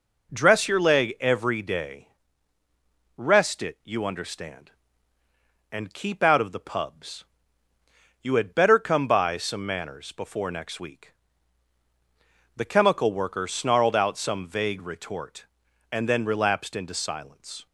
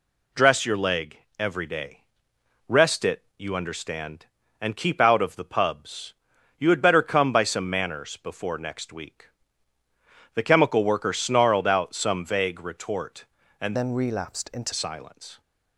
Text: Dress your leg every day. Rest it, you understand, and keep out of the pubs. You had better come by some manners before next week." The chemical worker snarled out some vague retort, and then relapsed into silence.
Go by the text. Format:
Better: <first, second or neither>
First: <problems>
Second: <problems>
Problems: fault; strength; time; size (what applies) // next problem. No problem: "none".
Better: first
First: none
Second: pauses between "leg" and "every"; slight; at 1.1 s; 0.20 s long // changes voice from "then" to "into"; from 13.7 to 14.7 s; 1.0 s long